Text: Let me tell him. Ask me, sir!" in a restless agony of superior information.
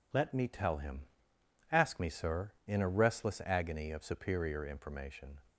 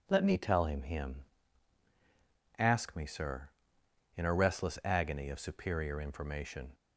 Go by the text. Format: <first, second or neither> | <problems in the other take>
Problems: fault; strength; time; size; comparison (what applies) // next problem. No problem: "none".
first | says "him" twice; at 0.8 s